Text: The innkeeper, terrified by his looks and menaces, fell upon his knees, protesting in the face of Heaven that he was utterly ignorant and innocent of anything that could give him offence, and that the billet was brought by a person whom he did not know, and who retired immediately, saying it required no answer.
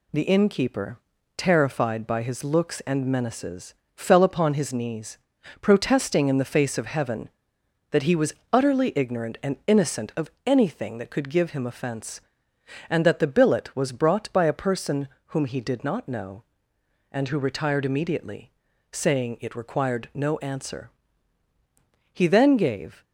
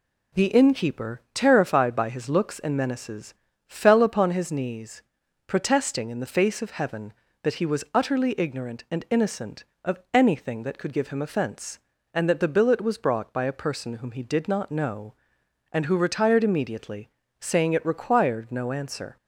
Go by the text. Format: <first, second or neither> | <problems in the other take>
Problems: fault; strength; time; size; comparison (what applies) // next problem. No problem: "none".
second | pauses between "was" and "utterly"; slight; at 8.3 s; 0.18 s long // pauses between "of" and "anything"; slight; at 10.2 s; 0.16 s long // pauses between "person" and "whom"; slight; at 15.0 s; 0.20 s long // goes on to say "He then gave"; noticeable; from 22.1 s on; 0.92 s long